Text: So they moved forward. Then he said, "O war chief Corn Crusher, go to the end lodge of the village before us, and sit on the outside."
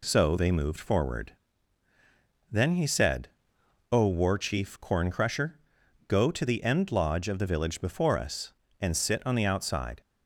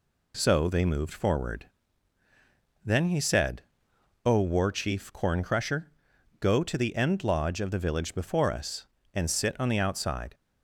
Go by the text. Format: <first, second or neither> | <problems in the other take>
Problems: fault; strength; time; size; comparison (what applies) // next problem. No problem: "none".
neither | none